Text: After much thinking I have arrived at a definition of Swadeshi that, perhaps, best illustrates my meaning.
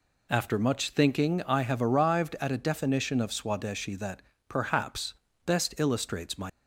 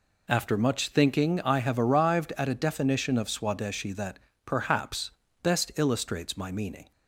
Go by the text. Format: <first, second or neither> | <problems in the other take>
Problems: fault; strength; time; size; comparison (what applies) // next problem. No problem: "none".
second | stops before "meaning"; at 6.4 s